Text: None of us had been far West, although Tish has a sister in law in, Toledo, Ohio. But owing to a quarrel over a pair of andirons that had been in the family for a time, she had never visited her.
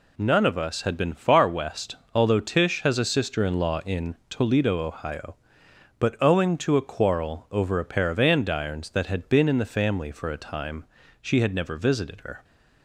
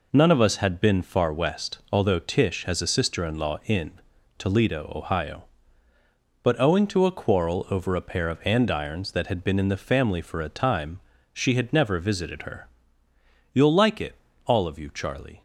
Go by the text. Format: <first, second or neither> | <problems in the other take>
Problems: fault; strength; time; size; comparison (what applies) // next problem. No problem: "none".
first | goes on to say "You'll like it all of you Charlie"; strong; from 13.5 s on; 1.9 s long